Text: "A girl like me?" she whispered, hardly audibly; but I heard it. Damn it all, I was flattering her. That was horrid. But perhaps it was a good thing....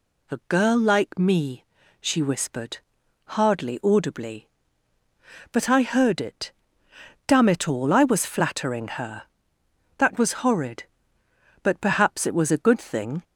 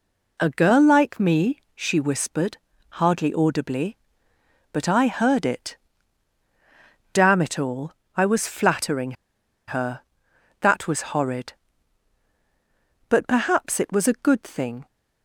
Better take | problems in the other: first | pauses between "flattering" and "her"; noticeable; at 9.1 s; 0.54 s long

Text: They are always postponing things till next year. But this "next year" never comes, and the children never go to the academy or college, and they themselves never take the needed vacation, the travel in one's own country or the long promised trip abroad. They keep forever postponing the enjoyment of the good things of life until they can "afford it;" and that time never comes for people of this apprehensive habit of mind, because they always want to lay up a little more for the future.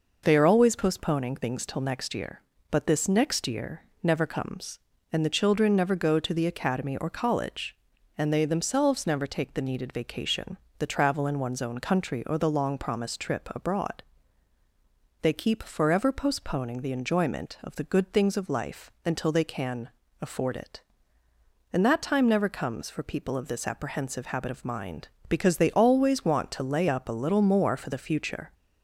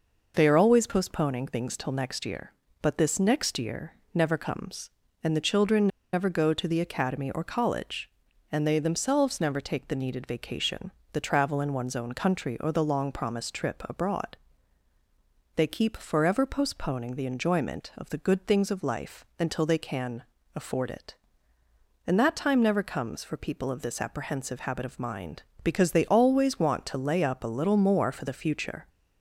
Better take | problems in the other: first | pauses between "year" and "never"; slight; at 3.9 s; 0.18 s long; slight in the first // pauses between "children" and "never"; slight; at 5.8 s; 0.25 s long // pauses between "can" and "afford"; slight; at 20.2 s; 0.32 s long; slight in the first

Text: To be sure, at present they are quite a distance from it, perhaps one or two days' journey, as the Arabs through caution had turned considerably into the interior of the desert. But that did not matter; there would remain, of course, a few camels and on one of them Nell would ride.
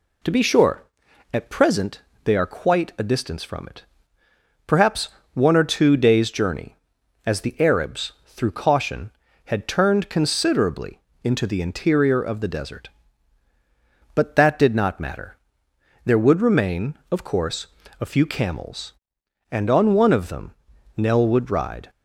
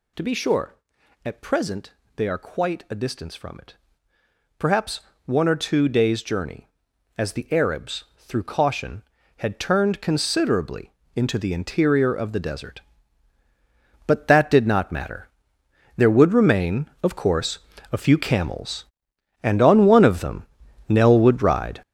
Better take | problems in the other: first | gets louder; strong; throughout; 10 dB // pauses between "present" and "they"; slight; at 1.9 s; 0.22 s long; slight in the first // pauses between "perhaps" and "one"; slight; at 5.0 s; 0.24 s long; slight in the first // pauses between "considerably" and "into"; slight; at 10.9 s; 0.24 s long; slight in the first // pauses between "them" and "Nell"; at 20.4 s; 0.44 s long; also in the first

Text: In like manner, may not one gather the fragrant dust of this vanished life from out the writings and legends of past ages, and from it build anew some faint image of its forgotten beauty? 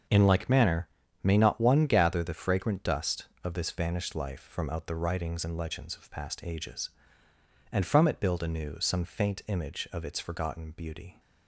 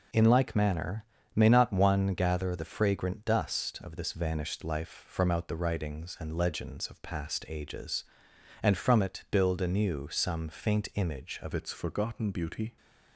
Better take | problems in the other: first | changes voice at "its"; from 11.5 s on; 1.2 s long

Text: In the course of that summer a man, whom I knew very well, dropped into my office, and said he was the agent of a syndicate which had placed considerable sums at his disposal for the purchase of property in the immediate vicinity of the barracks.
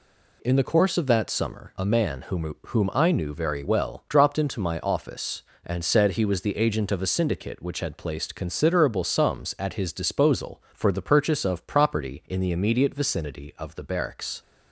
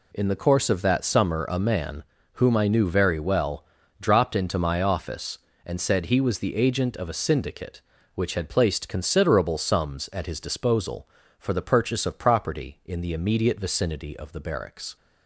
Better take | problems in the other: second | says "whom" twice; at 2.6 s

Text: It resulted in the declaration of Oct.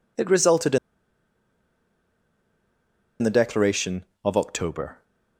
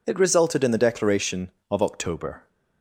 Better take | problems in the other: second | pauses between "in" and "the"; strong; at 0.7 s; 2.4 s long

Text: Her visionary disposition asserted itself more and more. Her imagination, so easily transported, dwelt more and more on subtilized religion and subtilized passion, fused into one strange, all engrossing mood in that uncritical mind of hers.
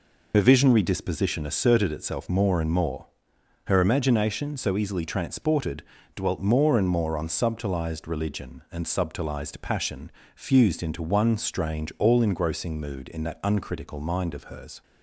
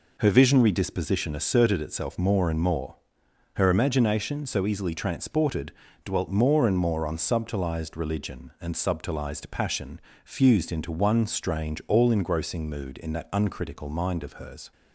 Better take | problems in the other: second | loses the start of "Her"; at 0.3 s; 45 ms

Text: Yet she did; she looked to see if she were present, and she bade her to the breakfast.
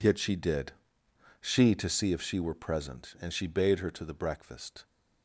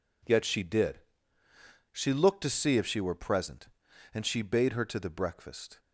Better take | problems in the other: second | skips "looked"; at 1.7 s

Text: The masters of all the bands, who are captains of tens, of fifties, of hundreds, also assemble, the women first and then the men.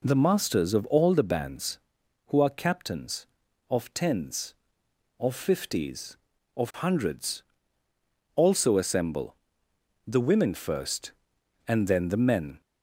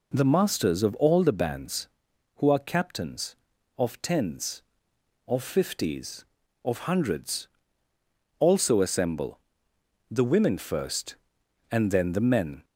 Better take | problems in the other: neither | none

